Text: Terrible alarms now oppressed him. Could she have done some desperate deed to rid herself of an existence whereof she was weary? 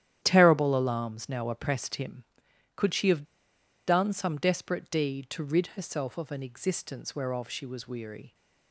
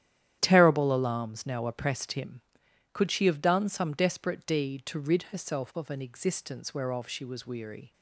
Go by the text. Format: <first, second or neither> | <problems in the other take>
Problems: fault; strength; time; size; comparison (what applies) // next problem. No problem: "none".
second | starts louder than the rest; strong; until 1.2 s; 11 dB; strong in the second // pauses between "have" and "done"; noticeable; at 3.2 s; 0.62 s long